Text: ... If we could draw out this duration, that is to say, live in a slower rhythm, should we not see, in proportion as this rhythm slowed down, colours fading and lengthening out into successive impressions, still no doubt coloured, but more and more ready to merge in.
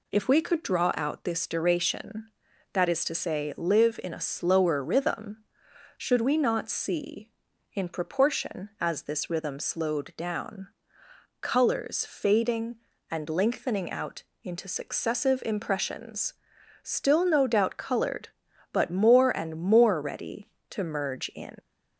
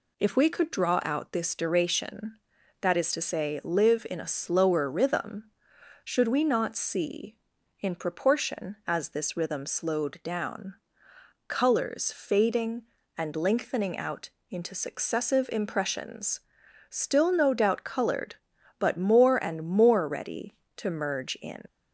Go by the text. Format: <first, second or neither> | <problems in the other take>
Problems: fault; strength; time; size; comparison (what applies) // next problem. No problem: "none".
neither | pauses between "out" and "into"; slight; the same in both